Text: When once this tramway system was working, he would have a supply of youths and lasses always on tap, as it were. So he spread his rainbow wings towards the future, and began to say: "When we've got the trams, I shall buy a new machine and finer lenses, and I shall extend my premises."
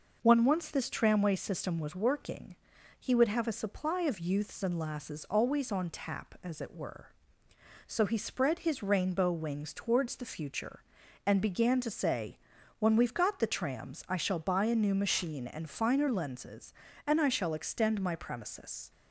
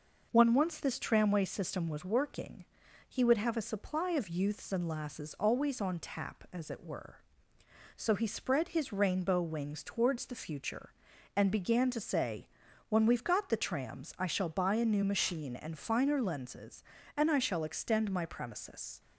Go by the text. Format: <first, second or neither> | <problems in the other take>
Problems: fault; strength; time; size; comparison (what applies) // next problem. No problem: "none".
neither | none